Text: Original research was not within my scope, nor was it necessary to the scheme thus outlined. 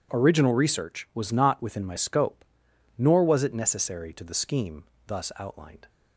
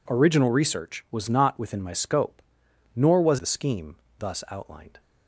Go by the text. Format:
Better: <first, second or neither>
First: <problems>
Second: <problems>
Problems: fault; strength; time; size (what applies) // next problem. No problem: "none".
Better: first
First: pauses between "scheme" and "thus"; slight; at 4.8 s; 0.22 s long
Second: skips "it necessary to"; at 3.3 s // pauses between "scheme" and "thus"; slight; at 3.9 s; 0.22 s long